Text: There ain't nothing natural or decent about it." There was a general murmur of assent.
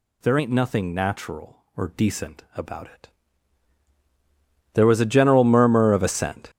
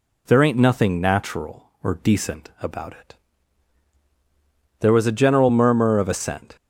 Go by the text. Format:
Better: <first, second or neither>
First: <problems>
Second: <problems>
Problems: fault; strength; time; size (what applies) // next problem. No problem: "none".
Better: second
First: gets louder; strong; throughout; 11.5 dB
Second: none